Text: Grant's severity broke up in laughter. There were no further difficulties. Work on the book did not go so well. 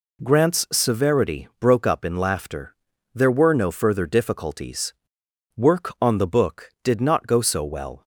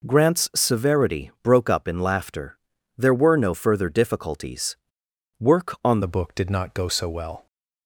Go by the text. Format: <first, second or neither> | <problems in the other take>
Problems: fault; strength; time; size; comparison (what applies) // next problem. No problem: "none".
first | changes voice at "the"; from 6.0 s on; 1.4 s long